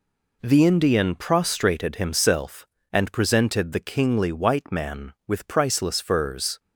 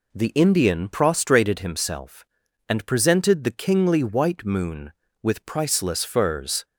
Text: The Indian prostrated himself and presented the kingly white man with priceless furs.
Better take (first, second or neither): first